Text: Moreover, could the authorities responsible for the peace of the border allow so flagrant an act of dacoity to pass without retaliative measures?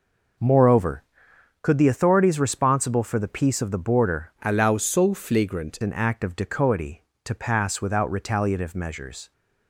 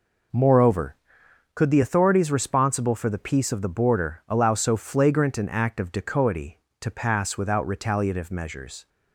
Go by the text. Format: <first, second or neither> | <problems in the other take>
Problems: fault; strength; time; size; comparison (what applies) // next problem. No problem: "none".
second | changes voice from "allow" to "flagrant"; from 4.4 to 5.7 s; 1.3 s long